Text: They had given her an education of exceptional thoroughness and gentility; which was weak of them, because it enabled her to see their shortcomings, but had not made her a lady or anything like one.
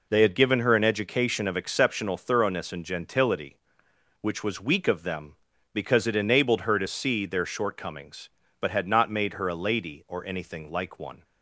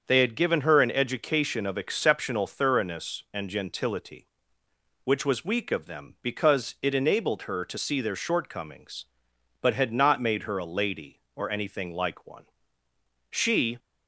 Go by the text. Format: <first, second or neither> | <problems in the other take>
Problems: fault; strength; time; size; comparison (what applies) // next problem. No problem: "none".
first | starts louder than the rest; until 1.0 s; 7 dB // goes on to say "She"; slight; from 13.3 s on; 0.48 s long